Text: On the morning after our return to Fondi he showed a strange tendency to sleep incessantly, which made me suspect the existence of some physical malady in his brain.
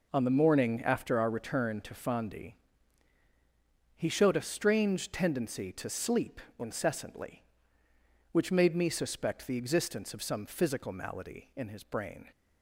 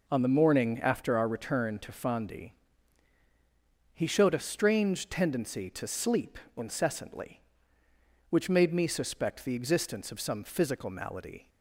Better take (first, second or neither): first